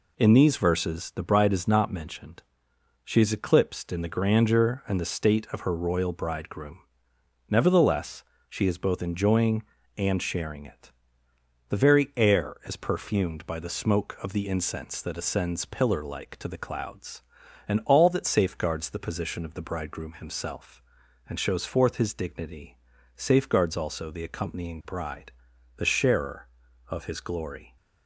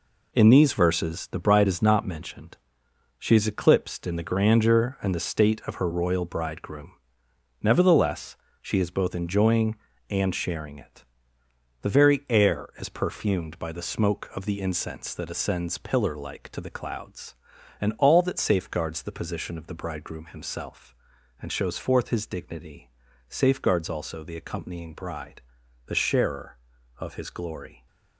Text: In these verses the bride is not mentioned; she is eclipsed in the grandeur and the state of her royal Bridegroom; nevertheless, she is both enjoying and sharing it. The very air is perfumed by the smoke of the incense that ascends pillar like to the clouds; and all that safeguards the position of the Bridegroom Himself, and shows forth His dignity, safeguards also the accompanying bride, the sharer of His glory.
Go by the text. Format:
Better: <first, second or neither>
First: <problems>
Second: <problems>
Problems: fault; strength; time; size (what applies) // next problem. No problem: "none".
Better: first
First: none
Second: gets quieter; strong; throughout; 8.5 dB